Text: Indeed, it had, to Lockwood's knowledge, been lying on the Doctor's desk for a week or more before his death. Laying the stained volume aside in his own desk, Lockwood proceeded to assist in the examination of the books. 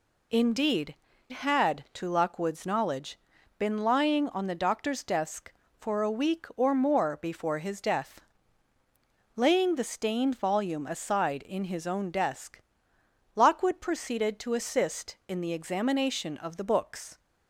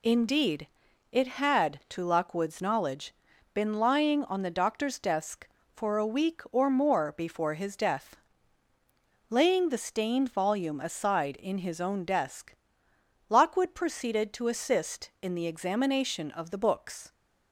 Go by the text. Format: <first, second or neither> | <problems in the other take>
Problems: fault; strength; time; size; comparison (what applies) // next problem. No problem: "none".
second | skips "it"; at 1.1 s